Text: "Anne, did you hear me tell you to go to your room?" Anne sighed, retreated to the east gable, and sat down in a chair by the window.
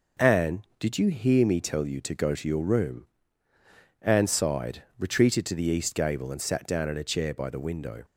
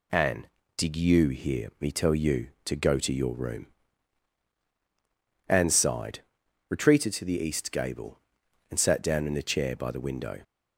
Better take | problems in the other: neither | none

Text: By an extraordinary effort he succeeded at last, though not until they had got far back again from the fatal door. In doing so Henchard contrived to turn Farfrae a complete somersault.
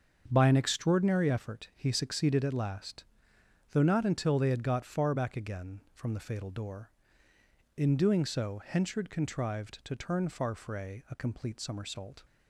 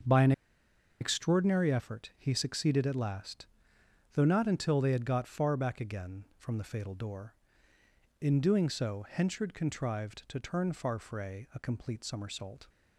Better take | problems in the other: first | starts louder than the rest; until 1.7 s; 7 dB; also in the first // pauses between "an" and "extraordinary"; noticeable; at 0.3 s; 0.69 s long

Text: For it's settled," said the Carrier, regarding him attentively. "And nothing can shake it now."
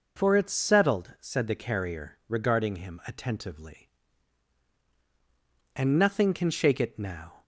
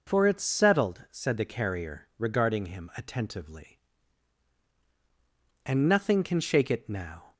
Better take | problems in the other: neither | none

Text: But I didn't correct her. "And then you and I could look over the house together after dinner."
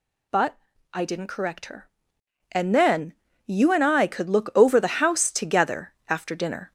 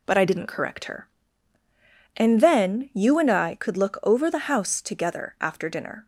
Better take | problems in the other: second | gets louder; throughout; 4 dB // pauses between "But" and "I"; slight; at 0.5 s; 0.34 s long // pauses between "then" and "you"; slight; at 3.1 s; 0.32 s long // pauses between "together" and "after"; slight; at 5.9 s; 0.16 s long

